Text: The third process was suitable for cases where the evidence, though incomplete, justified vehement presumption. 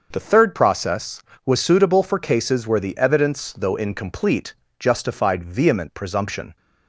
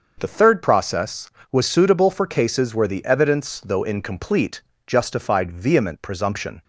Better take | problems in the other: neither | starts louder than the rest; the same in both

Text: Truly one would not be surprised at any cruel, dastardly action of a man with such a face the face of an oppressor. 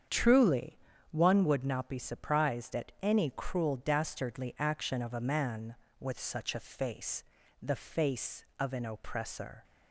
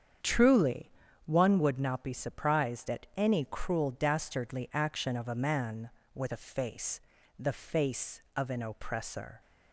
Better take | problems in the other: first | starts louder than the rest; strong; until 1.5 s; 8 dB; strong in the first // pauses between "Truly" and "one"; slight; at 0.9 s; 0.34 s long; slight in the first // skips "such"; at 6.3 s // pauses between "face" and "the"; at 7.0 s; 0.38 s long; also in the first

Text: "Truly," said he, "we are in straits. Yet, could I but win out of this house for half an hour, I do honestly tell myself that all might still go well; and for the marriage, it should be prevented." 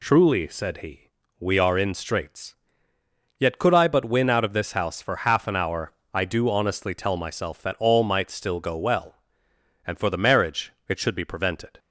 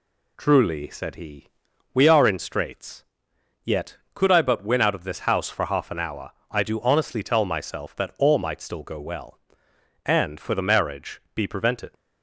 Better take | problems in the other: first | skips "it should"; at 11.2 s

